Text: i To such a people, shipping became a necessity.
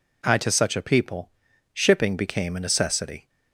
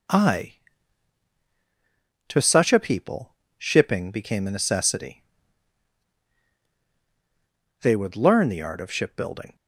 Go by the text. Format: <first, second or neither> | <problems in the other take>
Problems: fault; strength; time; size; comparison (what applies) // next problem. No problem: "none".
first | goes on to say "They would learn the art of shipbuilding"; strong; from 7.8 s on; 1.7 s long